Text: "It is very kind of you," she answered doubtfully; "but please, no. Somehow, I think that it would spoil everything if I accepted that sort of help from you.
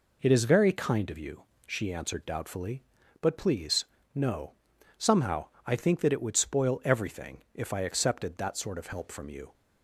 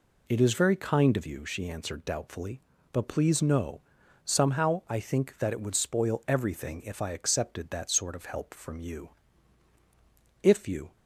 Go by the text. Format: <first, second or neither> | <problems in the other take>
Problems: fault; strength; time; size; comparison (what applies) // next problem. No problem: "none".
first | goes on to say "If you"; from 10.4 s on; 0.50 s long